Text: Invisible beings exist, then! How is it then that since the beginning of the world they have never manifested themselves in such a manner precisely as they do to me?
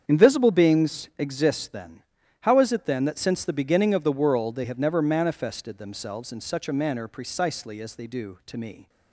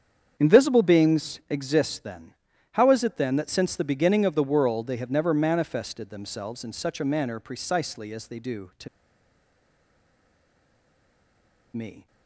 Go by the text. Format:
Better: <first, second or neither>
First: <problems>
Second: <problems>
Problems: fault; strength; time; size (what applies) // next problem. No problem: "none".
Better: first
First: starts louder than the rest; strong; until 1.0 s; 8 dB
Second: starts louder than the rest; strong; until 1.3 s; 8 dB // pauses between "to" and "me"; strong; at 8.8 s; 2.8 s long